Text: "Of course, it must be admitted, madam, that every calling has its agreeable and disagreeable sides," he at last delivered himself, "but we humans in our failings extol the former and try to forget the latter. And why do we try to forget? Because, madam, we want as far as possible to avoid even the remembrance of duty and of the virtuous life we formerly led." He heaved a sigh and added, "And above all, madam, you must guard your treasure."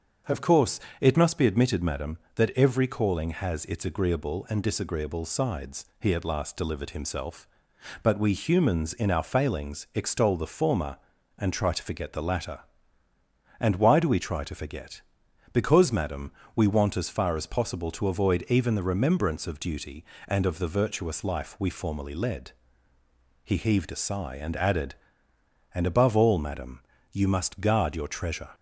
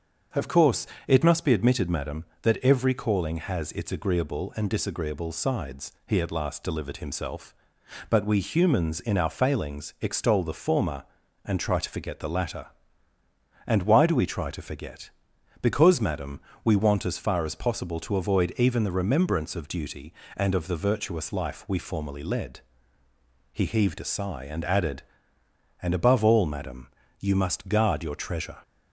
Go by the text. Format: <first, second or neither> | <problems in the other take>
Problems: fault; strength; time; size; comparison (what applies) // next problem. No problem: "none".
neither | starts louder than the rest; the same in both